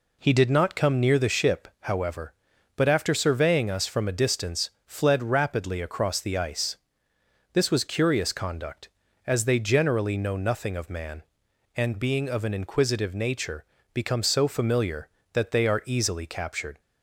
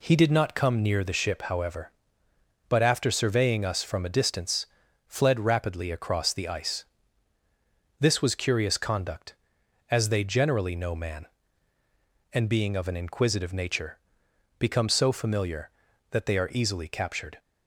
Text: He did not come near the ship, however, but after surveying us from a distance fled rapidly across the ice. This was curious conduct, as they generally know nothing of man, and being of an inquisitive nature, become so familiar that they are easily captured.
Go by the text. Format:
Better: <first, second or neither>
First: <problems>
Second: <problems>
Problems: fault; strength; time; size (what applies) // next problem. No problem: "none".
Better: first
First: pauses between "distance" and "fled"; slight; at 4.6 s; 0.16 s long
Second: pauses between "distance" and "fled"; at 4.6 s; 0.40 s long // skips "nothing of"; at 10.9 s